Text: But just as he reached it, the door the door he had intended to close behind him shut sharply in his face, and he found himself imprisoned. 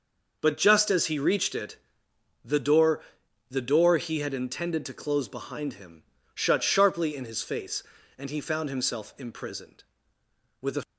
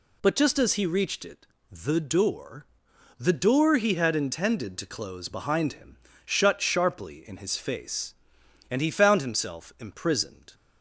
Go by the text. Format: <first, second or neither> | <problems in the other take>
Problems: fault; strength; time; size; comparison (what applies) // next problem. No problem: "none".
second | pauses between "door" and "the"; noticeable; at 3.0 s; 0.48 s long; noticeable in the second // pauses between "him" and "shut"; slight; at 6.0 s; 0.32 s long; slight in the second // goes on to say "With a"; slight; from 10.6 s on; 0.22 s long